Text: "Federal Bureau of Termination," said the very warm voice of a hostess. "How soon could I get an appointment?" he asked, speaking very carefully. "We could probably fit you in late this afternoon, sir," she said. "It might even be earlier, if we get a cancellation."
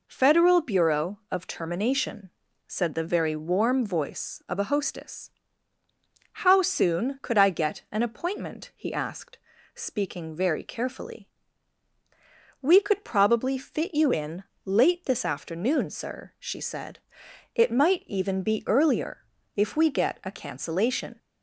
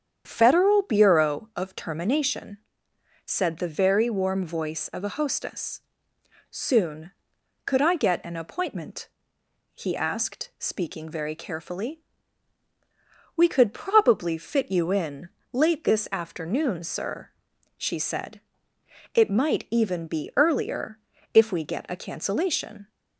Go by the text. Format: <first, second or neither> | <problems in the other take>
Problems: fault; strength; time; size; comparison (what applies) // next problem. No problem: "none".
first | starts louder than the rest; strong; until 1.2 s; 8 dB // skips "How"; at 6.1 s // pauses between "in" and "late"; slight; at 15.2 s; 0.24 s long; slight in the first